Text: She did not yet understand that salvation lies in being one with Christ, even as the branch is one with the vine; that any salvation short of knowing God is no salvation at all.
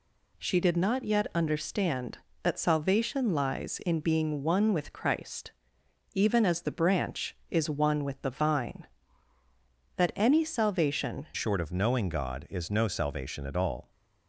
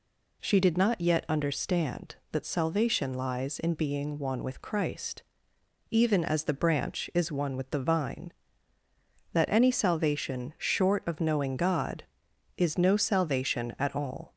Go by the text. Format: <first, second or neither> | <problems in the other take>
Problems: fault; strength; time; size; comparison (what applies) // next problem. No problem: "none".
second | changes voice at "short"; from 11.3 s on; 2.6 s long